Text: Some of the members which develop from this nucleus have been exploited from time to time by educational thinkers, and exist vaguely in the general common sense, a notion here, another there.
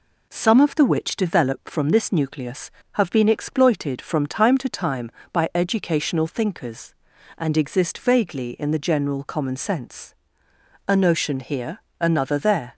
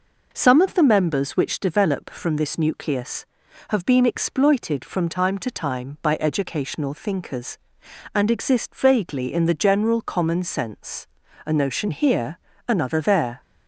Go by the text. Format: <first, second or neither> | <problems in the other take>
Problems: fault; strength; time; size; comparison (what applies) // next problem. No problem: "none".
second | skips "members"; at 0.8 s